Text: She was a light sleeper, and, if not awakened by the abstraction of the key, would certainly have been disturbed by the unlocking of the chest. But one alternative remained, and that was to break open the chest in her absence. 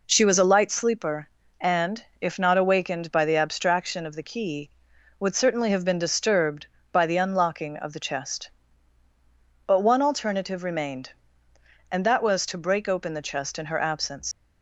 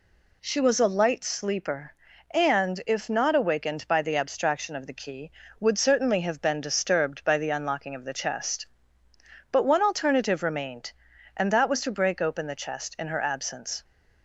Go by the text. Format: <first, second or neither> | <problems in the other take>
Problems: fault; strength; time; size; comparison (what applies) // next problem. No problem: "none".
second | leaves "absence" unfinished; at 14.3 s; 155 ms